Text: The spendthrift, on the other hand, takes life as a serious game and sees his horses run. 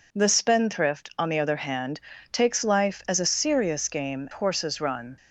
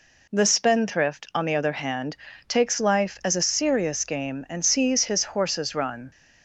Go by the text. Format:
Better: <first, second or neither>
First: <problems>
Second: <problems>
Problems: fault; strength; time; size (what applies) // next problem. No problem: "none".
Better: second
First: skips "and sees his"; at 4.2 s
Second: none